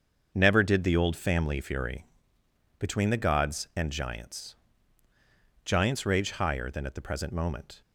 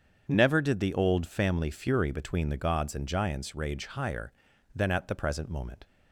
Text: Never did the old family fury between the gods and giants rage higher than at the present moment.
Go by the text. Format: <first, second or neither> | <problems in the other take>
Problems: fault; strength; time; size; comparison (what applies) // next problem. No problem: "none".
second | starts louder than the rest; until 1.3 s; 7 dB; strong in the second // pauses between "fury" and "between"; noticeable; at 2.0 s; 0.74 s long // says "giants" twice; at 5.6 s